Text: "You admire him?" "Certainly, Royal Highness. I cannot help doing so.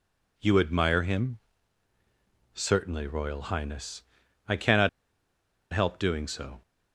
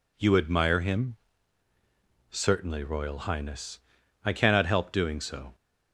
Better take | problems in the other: second | pauses between "cannot" and "help"; noticeable; at 4.8 s; 0.82 s long

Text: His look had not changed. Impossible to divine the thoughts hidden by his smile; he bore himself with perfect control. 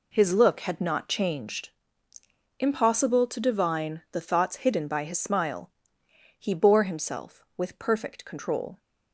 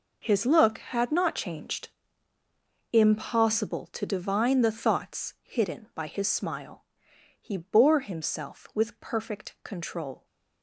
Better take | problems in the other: first | gets quieter; strong; throughout; 13 dB

